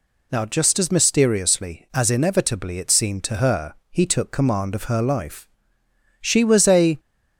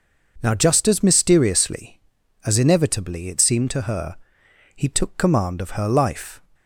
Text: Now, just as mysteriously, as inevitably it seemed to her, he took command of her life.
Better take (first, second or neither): second